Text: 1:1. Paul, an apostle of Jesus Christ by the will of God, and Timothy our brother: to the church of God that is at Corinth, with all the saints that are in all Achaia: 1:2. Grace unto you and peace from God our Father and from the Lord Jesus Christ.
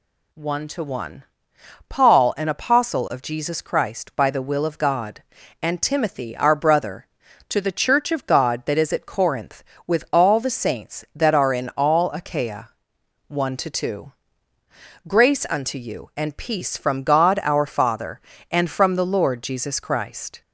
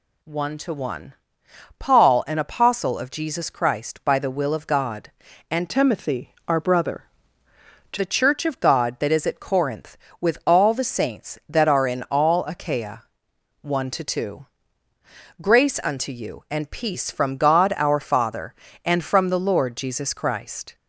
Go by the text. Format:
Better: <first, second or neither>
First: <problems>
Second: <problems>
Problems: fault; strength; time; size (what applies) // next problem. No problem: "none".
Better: first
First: none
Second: changes voice from "Timothy" to "to"; from 5.6 to 7.9 s; 2.3 s long // pauses between "Timothy" and "our"; slight; at 6.3 s; 0.16 s long